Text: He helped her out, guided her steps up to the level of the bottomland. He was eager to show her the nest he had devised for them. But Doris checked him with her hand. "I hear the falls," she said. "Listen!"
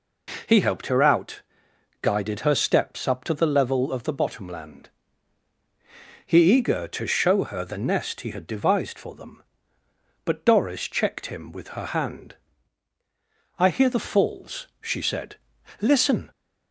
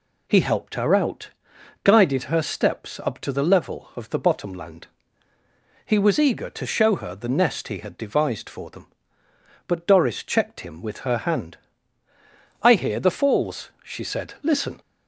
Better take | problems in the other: second | skips "was"; at 6.5 s

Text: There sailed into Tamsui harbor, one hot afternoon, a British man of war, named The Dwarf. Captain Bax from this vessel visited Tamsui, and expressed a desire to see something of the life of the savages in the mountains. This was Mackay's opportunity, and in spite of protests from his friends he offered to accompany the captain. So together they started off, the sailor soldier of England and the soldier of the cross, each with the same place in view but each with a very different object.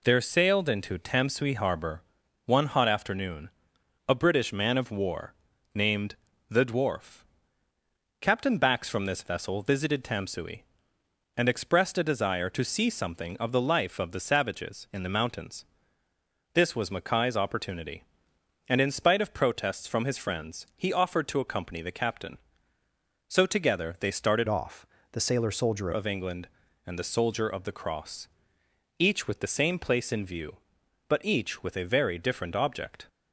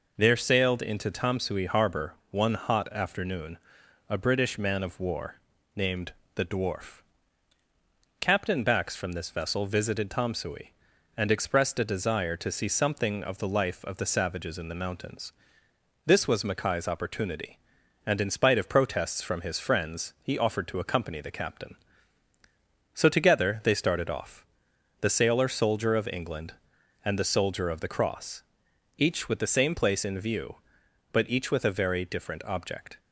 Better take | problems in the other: second | pauses between "named" and "The"; slight; at 6.1 s; 0.34 s long; slight in the second // changes voice from "off" to "soldier"; from 24.4 to 25.9 s; 1.5 s long

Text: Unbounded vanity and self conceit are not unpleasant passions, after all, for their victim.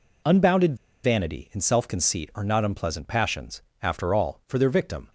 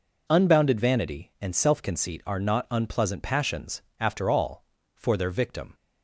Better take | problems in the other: second | pauses between "Unbounded" and "vanity"; slight; at 0.7 s; 0.27 s long

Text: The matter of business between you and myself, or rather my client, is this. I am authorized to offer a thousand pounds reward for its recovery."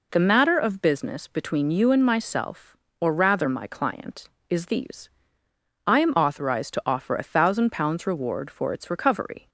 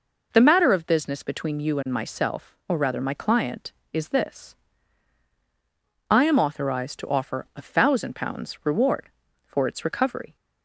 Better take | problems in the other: second | says "these" for "this"; at 4.6 s

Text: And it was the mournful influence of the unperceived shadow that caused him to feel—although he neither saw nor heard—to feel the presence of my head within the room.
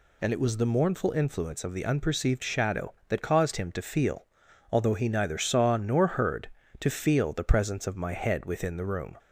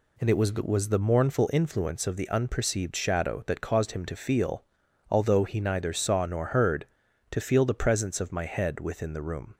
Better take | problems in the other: first | says "was" twice; at 0.5 s

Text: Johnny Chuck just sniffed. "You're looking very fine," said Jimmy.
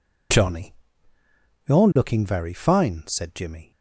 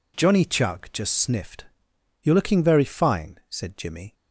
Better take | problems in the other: second | skips "Chuck just sniffed"; at 1.1 s

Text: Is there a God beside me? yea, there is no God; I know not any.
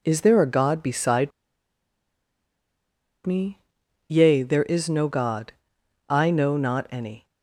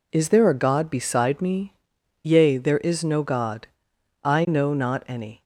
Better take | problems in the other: second | pauses between "beside" and "me"; strong; at 1.3 s; 1.9 s long

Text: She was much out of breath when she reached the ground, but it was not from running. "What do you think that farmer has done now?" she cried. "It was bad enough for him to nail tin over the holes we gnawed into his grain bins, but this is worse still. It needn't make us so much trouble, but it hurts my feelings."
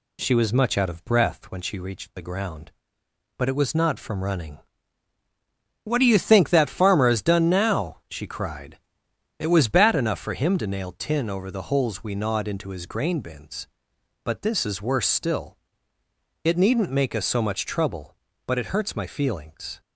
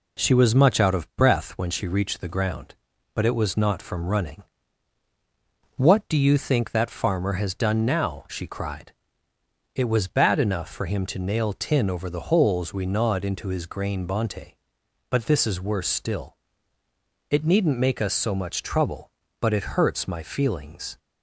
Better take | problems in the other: first | says "bonte" for "bins"; at 14.0 s

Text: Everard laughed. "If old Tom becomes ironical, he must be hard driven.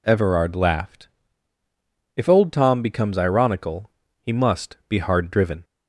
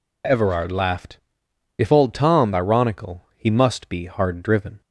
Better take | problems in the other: first | skips "becomes"; at 2.5 s

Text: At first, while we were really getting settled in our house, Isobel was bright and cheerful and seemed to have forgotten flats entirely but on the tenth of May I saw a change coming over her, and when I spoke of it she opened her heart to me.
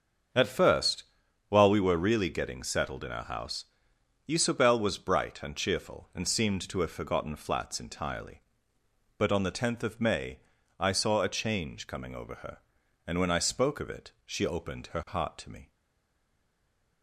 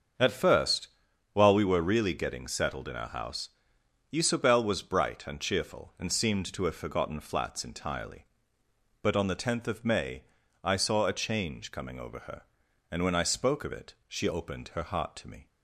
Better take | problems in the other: second | starts louder than the rest; until 1.7 s; 7 dB; also in the second // pauses between "May" and "I"; at 10.3 s; 0.40 s long; also in the second // stays silent after the last word; noticeable; from 15.7 s on; 1.3 s long

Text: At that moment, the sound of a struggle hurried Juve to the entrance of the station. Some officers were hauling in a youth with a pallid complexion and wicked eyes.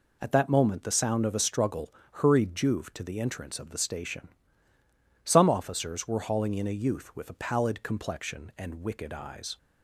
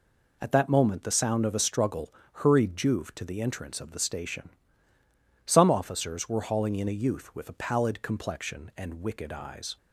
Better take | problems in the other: neither | pauses between "struggle" and "hurried"; slight; the same in both

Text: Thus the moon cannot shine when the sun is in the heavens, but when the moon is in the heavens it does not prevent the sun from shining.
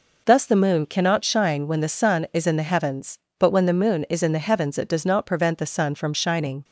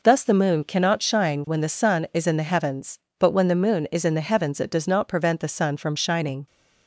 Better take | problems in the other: neither | none

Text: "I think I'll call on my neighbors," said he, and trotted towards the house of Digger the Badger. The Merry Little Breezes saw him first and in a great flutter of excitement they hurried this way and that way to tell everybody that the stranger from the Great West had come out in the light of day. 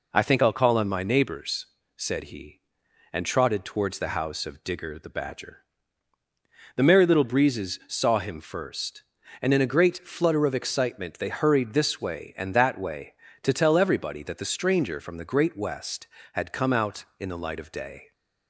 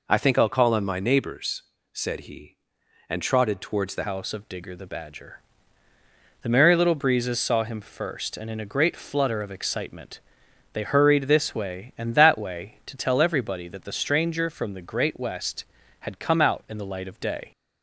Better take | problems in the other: first | changes voice at "house"; from 4.0 s on; 13.5 s long // pauses between "excitement" and "they"; noticeable; at 10.2 s; 0.52 s long

